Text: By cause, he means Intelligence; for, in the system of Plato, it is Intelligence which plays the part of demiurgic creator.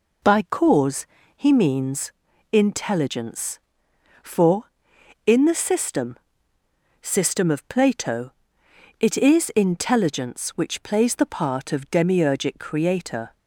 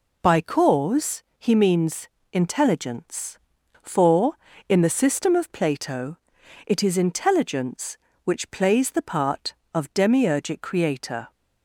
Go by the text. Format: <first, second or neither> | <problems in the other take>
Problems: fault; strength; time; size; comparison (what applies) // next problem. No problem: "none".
second | pauses between "means" and "Intelligence"; at 2.1 s; 0.42 s long; slight in the second // says "system" twice; at 7.0 s